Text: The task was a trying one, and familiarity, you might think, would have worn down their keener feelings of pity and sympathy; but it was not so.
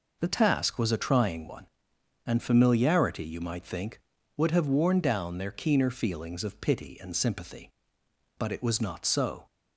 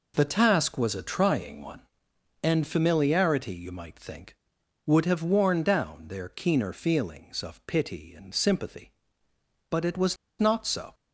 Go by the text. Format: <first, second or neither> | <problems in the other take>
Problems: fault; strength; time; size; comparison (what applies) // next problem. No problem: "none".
first | pauses between "was" and "not"; slight; at 10.1 s; 0.23 s long